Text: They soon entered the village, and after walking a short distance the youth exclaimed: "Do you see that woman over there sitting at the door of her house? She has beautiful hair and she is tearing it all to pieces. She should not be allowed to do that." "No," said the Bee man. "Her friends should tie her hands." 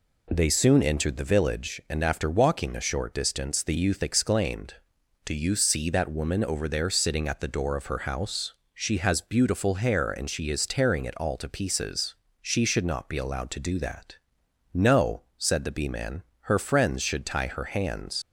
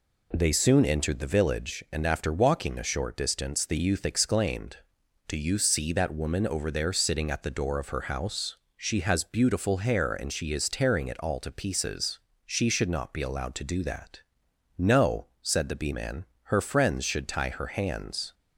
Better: second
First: leaves "hands" unfinished; at 18.2 s; 90 ms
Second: none

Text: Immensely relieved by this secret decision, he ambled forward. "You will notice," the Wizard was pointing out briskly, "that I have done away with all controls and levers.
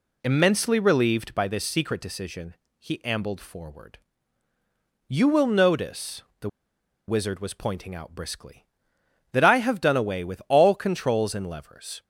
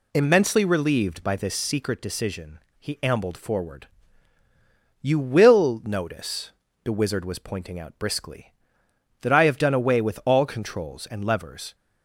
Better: second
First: pauses between "the" and "Wizard"; noticeable; at 6.4 s; 0.59 s long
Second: none

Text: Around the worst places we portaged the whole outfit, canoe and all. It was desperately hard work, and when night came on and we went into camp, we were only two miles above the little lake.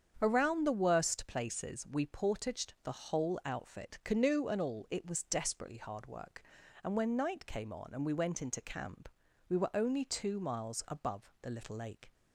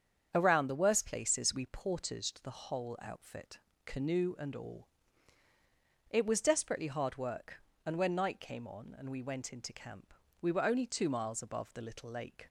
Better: neither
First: starts louder than the rest; strong; until 1.2 s; 8 dB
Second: starts louder than the rest; strong; until 1.3 s; 8 dB

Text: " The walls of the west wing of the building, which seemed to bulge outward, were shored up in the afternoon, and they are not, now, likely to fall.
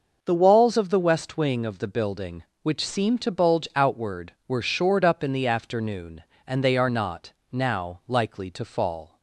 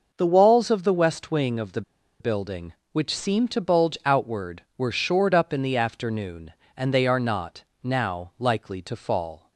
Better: first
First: none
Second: pauses between "the" and "building"; at 1.8 s; 0.39 s long

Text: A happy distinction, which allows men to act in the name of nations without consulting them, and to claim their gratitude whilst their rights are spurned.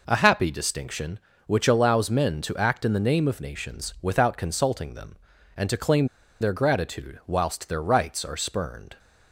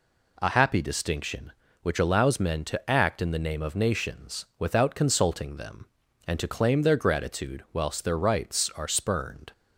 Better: second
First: pauses between "claim" and "their"; slight; at 6.0 s; 0.35 s long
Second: none

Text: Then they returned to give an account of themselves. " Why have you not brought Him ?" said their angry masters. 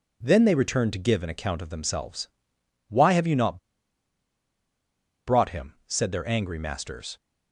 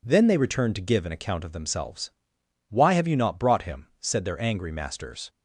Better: second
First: pauses between "not" and "brought"; strong; at 3.5 s; 1.6 s long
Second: none

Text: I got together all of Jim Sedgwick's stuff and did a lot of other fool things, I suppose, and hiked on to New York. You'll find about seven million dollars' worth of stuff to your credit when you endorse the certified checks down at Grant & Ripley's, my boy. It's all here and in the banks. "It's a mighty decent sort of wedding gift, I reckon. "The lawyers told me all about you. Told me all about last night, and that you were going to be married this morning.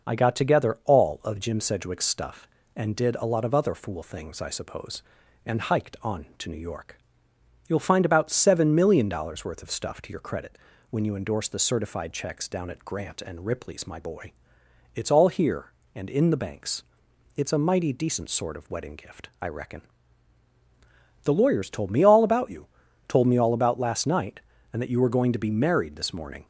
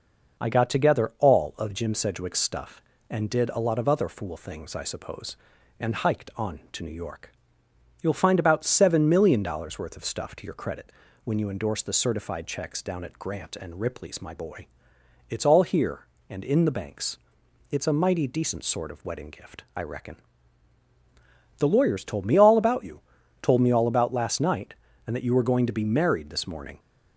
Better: neither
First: pauses between "credit" and "when"; slight; at 10.5 s; 0.32 s long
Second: pauses between "credit" and "when"; slight; at 10.9 s; 0.32 s long

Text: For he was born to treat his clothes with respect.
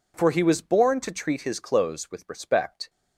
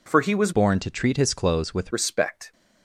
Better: first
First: none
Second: changes voice from "born" to "with"; from 0.5 to 1.9 s; 1.4 s long

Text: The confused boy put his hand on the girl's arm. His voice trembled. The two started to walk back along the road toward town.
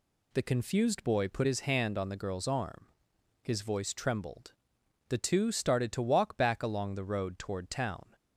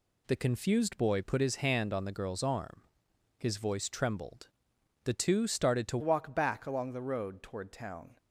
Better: first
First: none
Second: changes voice at "walk"; from 6.0 s on; 2.1 s long

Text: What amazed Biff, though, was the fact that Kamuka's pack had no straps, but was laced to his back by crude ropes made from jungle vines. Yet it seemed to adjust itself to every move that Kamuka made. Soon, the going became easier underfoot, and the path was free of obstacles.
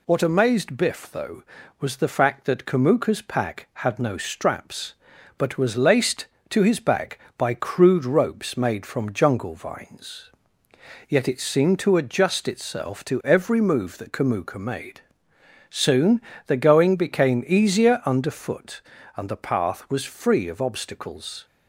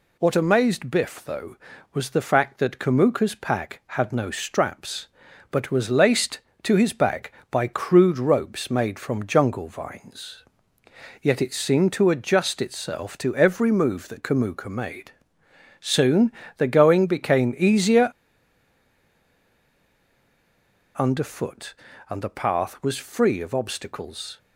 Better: first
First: none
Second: pauses between "easier" and "underfoot"; strong; at 18.1 s; 2.8 s long

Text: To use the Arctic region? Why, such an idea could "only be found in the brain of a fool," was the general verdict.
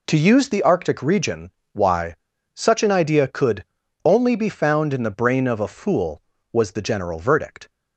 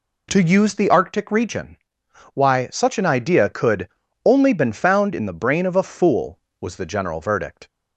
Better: first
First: pauses between "could" and "only"; at 3.6 s; 0.38 s long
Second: pauses between "could" and "only"; slight; at 3.8 s; 0.36 s long // says "been" for "be"; at 4.5 s

